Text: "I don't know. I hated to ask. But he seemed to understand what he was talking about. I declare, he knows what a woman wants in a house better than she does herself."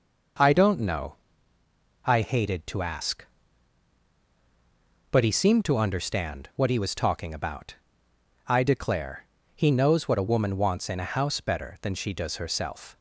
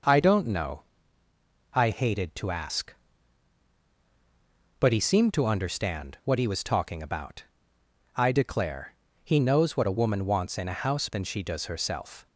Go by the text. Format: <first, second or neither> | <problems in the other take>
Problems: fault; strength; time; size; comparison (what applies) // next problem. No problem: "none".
first | skips "better"; at 11.0 s